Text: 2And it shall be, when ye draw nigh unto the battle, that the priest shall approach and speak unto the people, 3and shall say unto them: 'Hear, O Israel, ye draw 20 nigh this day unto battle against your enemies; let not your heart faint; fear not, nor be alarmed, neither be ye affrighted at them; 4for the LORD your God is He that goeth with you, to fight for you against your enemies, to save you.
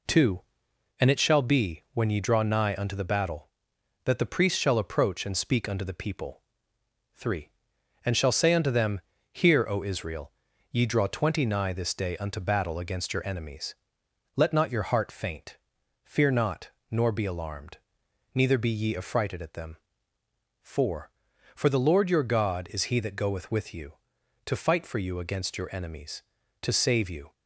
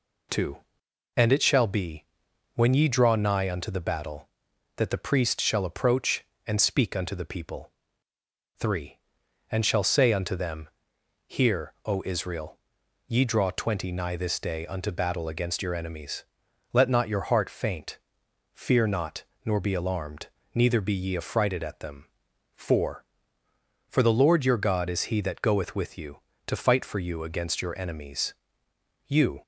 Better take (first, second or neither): first